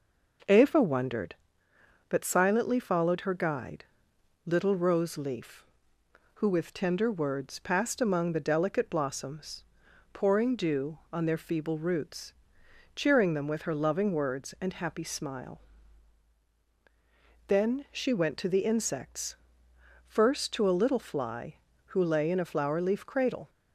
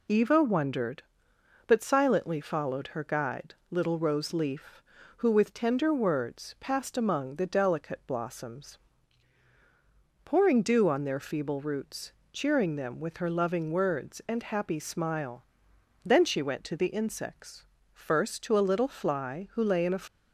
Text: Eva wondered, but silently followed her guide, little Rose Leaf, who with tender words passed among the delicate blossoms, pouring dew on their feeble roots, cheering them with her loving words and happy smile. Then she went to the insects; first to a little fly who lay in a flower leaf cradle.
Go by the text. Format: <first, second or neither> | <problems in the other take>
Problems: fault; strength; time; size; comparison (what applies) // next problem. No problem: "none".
first | stops before "flower leaf cradle"; at 20.0 s